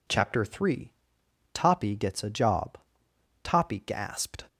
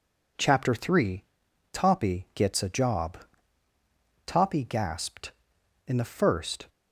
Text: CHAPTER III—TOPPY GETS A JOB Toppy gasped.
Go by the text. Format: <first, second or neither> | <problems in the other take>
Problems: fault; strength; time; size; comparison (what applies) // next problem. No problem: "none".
first | pauses between "JOB" and "Toppy"; at 3.2 s; 1.0 s long; noticeable in the first // goes on to say "In the first"; noticeable; from 5.8 s on; 0.84 s long